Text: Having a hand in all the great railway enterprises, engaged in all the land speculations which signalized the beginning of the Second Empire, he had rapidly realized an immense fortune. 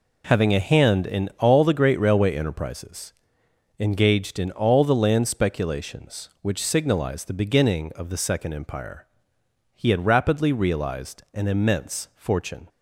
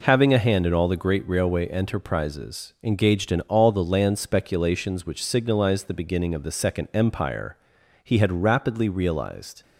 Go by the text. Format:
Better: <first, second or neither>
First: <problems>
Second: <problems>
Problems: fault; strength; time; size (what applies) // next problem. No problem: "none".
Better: first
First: none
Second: stops before "an immense fortune"; at 9.6 s